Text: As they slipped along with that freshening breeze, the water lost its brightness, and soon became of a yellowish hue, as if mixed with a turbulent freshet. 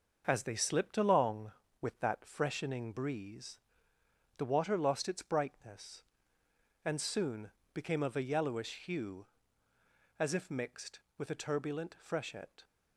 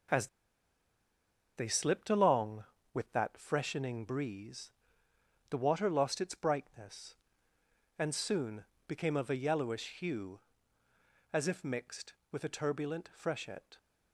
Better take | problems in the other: first | starts louder than the rest; until 2.4 s; 6.5 dB; also in the first // pauses between "As" and "they"; strong; at 0.2 s; 1.2 s long // pauses between "soon" and "became"; slight; at 8.6 s; 0.24 s long; slight in the first

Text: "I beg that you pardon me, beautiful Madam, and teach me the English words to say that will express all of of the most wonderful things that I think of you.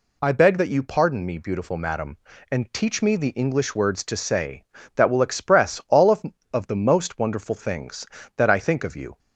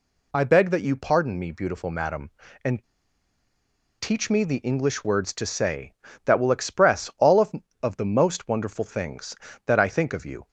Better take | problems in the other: first | pauses between "and" and "teach"; at 2.8 s; 1.1 s long

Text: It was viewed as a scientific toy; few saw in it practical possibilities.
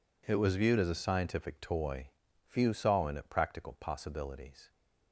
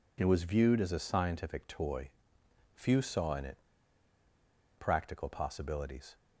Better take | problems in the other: first | pauses between "it" and "practical"; at 3.5 s; 1.2 s long

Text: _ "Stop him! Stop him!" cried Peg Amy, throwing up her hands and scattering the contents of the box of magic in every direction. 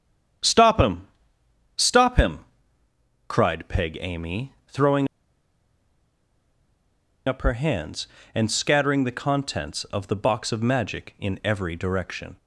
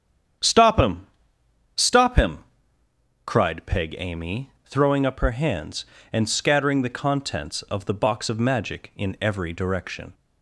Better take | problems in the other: second | starts louder than the rest; strong; until 2.1 s; 9 dB; strong in the second // pauses between "throwing" and "up"; strong; at 5.0 s; 2.1 s long

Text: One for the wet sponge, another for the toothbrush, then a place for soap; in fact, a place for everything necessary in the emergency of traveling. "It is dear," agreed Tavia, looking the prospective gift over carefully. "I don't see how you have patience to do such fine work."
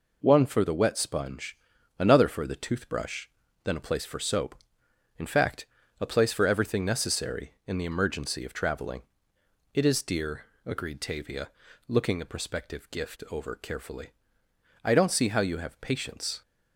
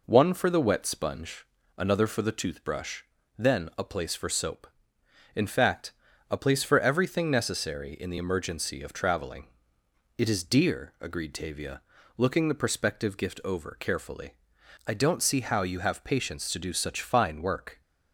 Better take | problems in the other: second | stops before "to do such fine work"; at 16.4 s

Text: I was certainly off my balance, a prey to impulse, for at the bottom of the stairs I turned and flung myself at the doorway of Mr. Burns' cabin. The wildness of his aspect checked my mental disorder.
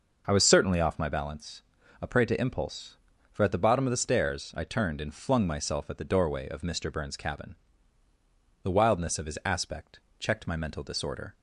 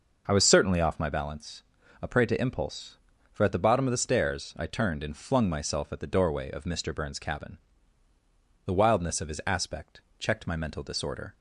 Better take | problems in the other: neither | pauses between "aspect" and "checked"; slight; the same in both

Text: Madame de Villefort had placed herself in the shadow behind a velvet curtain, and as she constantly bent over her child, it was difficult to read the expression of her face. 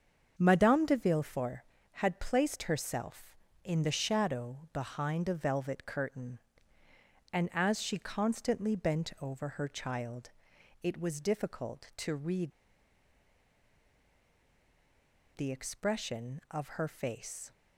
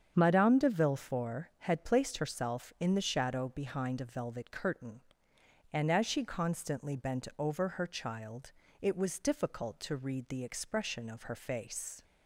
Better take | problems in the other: second | starts louder than the rest; until 1.3 s; 7 dB; strong in the second // pauses between "read" and "the"; strong; at 12.5 s; 2.8 s long

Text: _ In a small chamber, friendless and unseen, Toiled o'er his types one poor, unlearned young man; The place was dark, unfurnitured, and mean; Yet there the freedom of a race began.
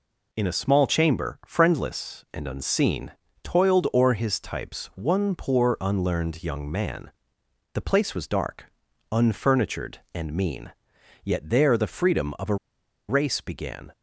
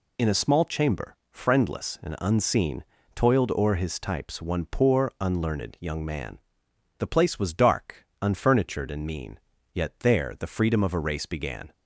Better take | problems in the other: second | pauses between "a" and "race"; noticeable; at 12.5 s; 0.53 s long

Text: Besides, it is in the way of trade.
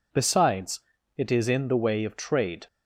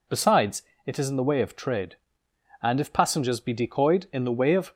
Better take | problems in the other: first | goes on to say "And if passengers be decoyed in the way of"; strong; from 2.6 s on; 2.1 s long

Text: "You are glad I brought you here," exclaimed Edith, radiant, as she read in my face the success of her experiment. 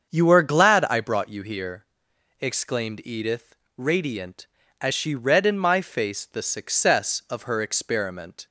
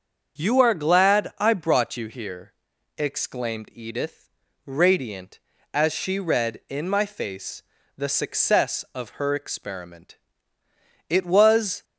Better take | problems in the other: first | starts louder than the rest; until 1.4 s; 7 dB; also in the first // pauses between "face" and "the"; slight; at 7.6 s; 0.34 s long // goes on to say "It was"; noticeable; from 11.0 s on; 0.76 s long

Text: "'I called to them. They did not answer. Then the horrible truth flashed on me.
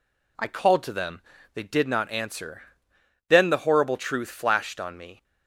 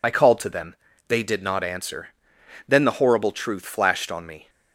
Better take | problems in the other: first | loses the start of "I"; at 0.0 s; 55 ms

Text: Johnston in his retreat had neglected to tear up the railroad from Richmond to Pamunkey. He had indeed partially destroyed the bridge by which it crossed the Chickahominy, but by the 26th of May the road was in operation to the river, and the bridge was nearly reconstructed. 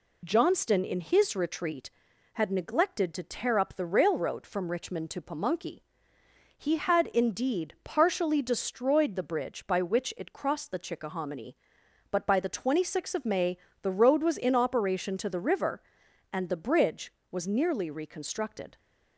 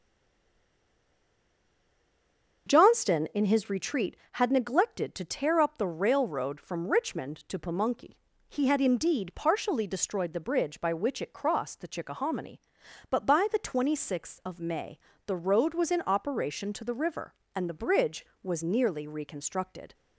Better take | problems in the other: first | stays silent before the first word; strong; until 2.6 s; 2.6 s long // starts louder than the rest; until 3.7 s; 7 dB // pauses between "May" and "the"; slight; at 14.9 s; 0.30 s long; slight in the first

